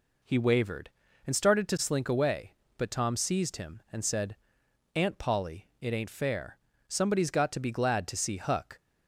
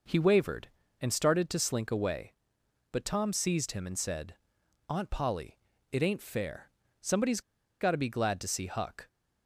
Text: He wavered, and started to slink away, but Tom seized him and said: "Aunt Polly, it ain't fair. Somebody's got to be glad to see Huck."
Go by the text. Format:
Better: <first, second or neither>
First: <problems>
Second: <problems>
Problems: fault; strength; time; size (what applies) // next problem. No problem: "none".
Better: first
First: none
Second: pauses between "Somebody's" and "got"; at 7.4 s; 0.40 s long